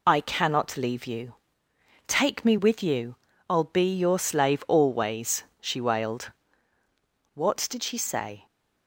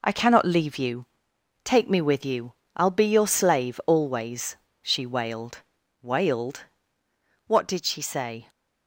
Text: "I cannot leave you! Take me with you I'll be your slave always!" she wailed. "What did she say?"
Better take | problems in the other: first | pauses between "you" and "I'll"; slight; at 2.5 s; 0.22 s long; slight in the first // says "wailed" twice; at 6.0 s

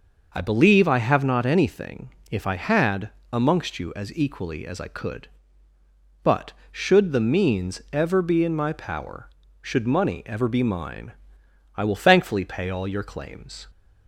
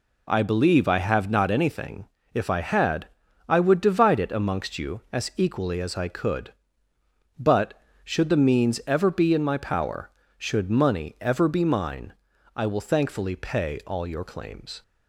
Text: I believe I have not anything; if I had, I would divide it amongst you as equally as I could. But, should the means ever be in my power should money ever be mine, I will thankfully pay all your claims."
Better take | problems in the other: second | skips "I would divide it"; at 3.2 s

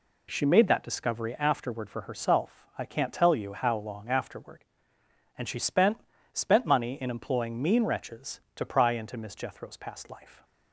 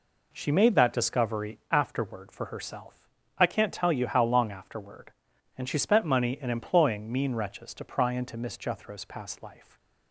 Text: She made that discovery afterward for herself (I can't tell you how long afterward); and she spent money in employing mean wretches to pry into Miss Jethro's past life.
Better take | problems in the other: second | says "spent" twice; at 6.3 s

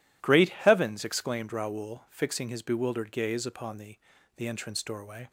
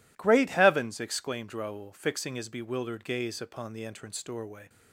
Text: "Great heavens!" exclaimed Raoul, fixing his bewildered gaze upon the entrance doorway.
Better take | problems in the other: second | says "the" twice; at 4.3 s

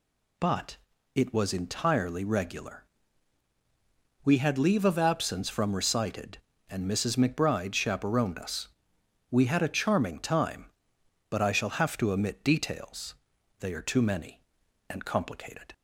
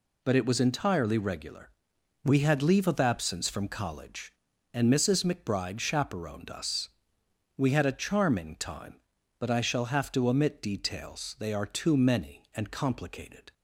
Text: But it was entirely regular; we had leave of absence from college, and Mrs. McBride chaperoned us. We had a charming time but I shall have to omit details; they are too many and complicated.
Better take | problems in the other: second | pauses between "But" and "it"; at 0.7 s; 0.38 s long // says "recited" for "college"; at 5.7 s

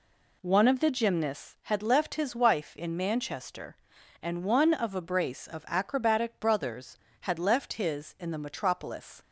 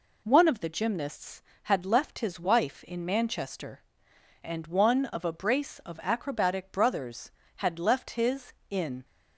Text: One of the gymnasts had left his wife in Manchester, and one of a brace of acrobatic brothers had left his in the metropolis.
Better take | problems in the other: first | stops before "the metropolis"; at 9.0 s

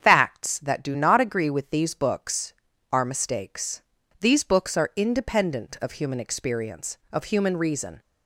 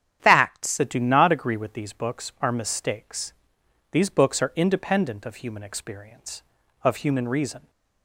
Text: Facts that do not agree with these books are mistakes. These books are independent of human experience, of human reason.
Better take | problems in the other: first | starts louder than the rest; strong; until 1.2 s; 9.5 dB; strong in the first // changes voice at "that"; from 0.7 s on; 6.9 s long

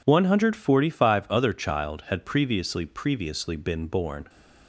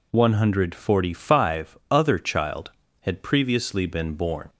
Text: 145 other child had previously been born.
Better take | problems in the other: second | says "previously" twice; at 2.8 s

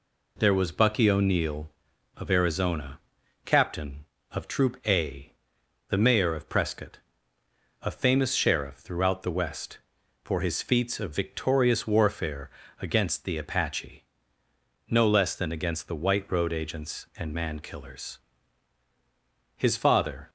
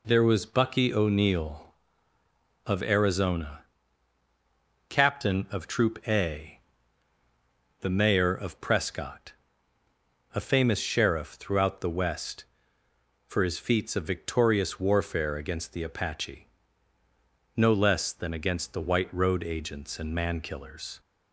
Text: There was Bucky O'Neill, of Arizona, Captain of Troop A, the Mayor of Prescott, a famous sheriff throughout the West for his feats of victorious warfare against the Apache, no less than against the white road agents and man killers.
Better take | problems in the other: second | pauses between "warfare" and "against"; slight; at 12.5 s; 0.28 s long // goes on to say "His father"; noticeable; from 19.5 s on; 0.74 s long

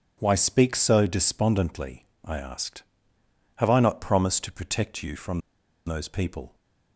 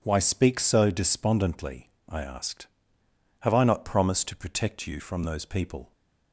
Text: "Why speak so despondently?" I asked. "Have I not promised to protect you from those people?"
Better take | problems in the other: second | pauses between "from" and "those"; noticeable; at 5.3 s; 0.47 s long

